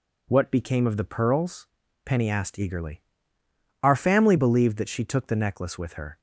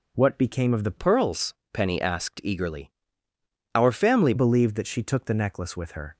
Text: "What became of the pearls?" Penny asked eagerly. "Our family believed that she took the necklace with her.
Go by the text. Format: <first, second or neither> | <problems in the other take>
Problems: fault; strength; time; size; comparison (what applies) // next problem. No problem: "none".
first | changes voice from "pearls" to "family"; from 0.9 to 4.3 s; 3.4 s long